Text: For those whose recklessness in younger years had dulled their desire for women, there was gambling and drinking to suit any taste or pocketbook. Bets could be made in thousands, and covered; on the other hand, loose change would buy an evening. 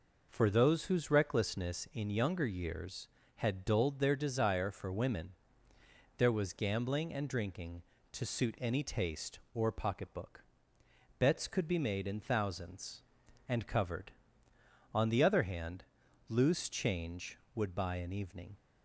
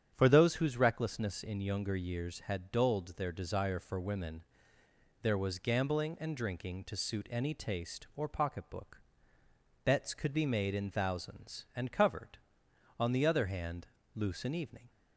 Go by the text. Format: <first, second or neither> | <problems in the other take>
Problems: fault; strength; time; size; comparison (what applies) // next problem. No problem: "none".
first | starts louder than the rest; strong; until 1.1 s; 9 dB // skips "change would buy"; at 14.4 s